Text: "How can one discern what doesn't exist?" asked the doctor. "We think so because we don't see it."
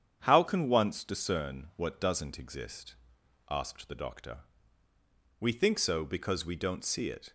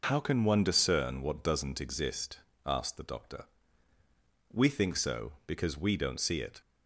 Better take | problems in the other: second | starts louder than the rest; strong; until 1.2 s; 8.5 dB // says "once" for "one"; at 0.6 s

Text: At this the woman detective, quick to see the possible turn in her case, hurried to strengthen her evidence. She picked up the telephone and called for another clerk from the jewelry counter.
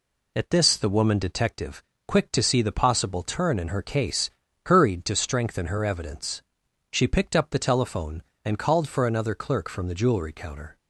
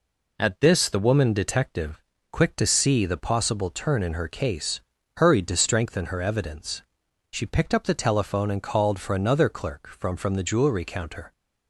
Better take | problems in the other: first | says "from" twice; at 10.1 s

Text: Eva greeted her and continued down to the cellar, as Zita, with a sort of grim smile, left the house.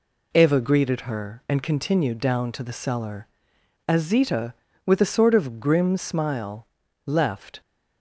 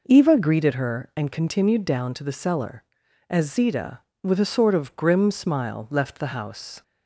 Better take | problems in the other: second | stops before "the house"; at 7.6 s

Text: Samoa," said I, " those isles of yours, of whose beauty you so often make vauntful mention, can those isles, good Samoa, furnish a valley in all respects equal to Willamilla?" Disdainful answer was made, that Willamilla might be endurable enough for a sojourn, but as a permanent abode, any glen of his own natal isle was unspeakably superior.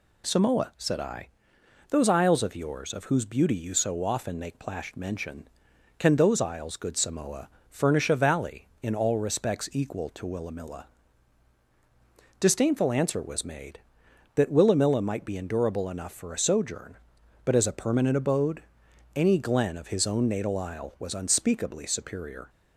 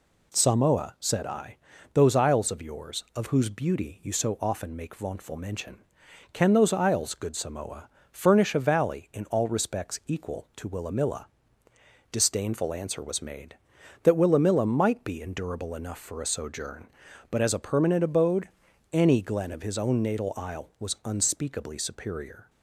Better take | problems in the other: second | says "plashed" for "vauntful"; at 4.5 s

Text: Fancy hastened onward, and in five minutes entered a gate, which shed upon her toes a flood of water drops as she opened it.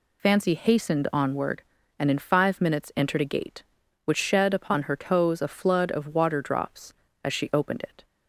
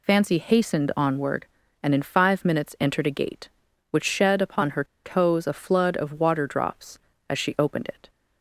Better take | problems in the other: first | pauses between "her" and "toes"; slight; at 4.8 s; 0.20 s long

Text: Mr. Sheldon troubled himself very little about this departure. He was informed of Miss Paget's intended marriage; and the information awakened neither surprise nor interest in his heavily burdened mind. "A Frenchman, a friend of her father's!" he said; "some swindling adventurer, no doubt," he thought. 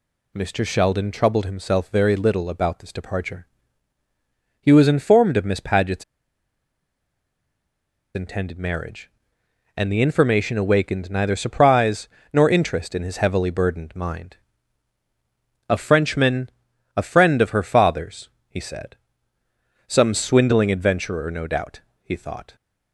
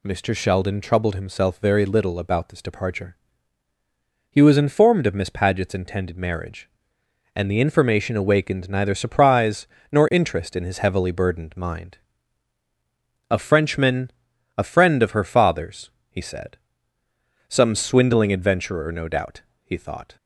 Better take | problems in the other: second | pauses between "Paget's" and "intended"; strong; at 6.0 s; 2.1 s long // pauses between "surprise" and "nor"; slight; at 12.0 s; 0.24 s long; slight in the second

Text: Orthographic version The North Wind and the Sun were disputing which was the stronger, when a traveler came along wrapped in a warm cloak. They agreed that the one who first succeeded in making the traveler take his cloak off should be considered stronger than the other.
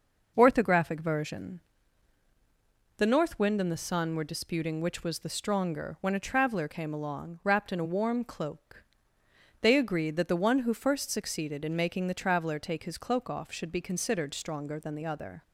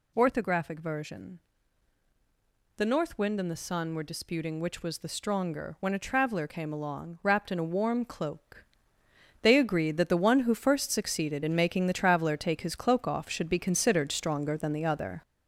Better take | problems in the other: first | gets louder; noticeable; throughout; 6 dB // pauses between "version" and "The"; strong; at 1.3 s; 1.3 s long; strong in the first

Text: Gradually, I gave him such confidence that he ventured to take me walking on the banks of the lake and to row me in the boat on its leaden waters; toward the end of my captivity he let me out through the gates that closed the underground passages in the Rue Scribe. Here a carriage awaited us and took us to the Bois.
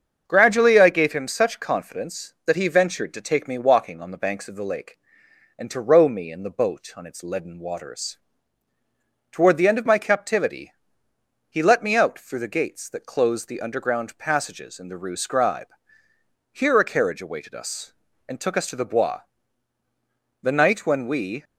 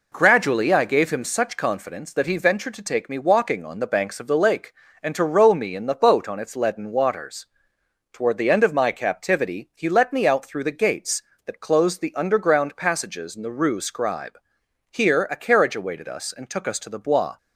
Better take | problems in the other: second | starts louder than the rest; until 1.2 s; 6.5 dB // pauses between "captivity" and "he"; noticeable; at 10.7 s; 0.76 s long // goes on to say "The night when we"; noticeable; from 20.4 s on; 1.0 s long

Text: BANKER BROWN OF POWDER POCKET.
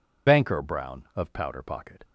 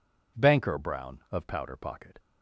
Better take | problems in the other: second | loses the start of "BANKER"; at 0.2 s; 80 ms

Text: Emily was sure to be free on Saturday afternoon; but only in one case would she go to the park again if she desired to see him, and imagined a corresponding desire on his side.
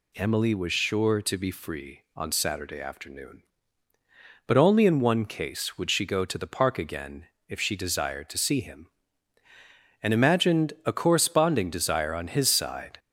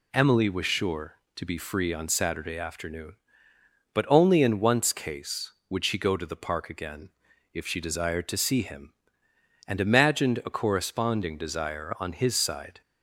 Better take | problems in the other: first | says "once" for "one"; at 4.5 s // pauses between "again" and "if"; at 7.1 s; 0.42 s long; slight in the first

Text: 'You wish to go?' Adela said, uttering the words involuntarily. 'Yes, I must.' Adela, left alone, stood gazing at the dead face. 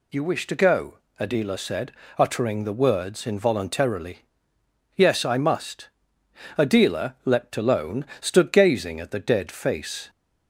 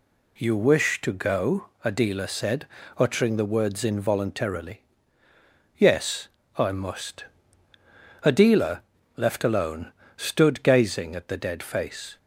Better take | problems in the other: second | says "leapt" for "left"; at 7.2 s

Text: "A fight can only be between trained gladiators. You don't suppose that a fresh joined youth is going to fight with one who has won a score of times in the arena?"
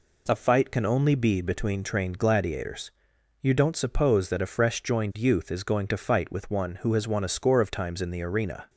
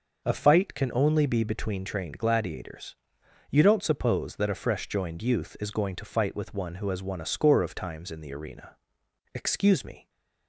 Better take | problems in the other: first | goes on to say "Excuse me"; noticeable; from 9.3 s on; 0.76 s long

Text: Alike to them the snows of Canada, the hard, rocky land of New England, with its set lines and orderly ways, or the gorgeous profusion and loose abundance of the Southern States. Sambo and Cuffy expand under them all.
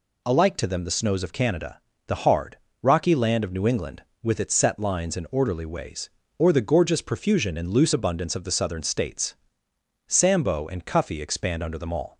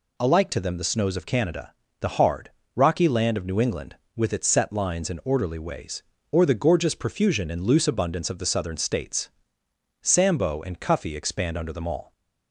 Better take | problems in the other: neither | none

